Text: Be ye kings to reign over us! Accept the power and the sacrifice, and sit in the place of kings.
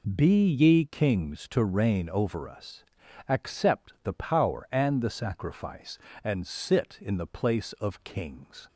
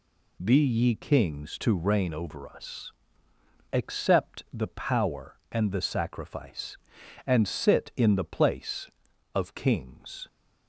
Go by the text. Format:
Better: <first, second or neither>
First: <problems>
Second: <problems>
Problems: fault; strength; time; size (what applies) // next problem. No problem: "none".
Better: neither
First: none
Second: none